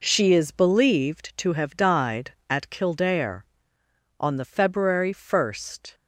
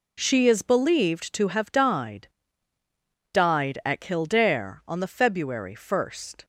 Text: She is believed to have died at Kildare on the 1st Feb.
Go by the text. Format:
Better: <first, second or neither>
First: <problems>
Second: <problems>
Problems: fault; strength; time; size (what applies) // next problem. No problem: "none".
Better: first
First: none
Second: says "died" twice; at 3.3 s